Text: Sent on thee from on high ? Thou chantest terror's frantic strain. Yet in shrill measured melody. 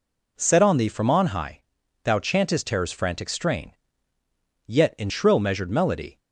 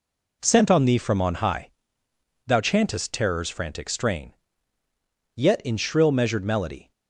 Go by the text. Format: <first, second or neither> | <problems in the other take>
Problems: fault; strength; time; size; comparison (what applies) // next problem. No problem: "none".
second | says "Set" for "Sent"; at 0.3 s